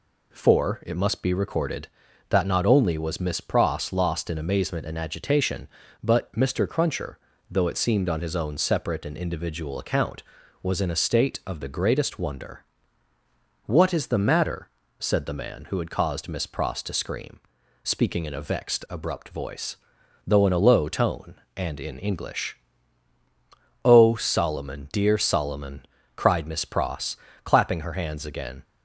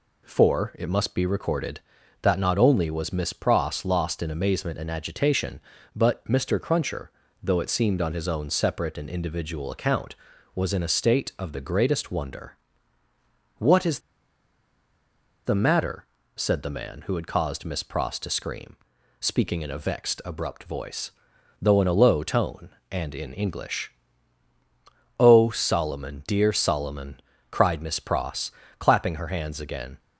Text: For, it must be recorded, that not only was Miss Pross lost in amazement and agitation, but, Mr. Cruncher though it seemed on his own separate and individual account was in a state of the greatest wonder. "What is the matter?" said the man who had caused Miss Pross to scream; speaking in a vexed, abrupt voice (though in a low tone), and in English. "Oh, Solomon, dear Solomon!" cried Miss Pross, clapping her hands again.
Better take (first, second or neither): first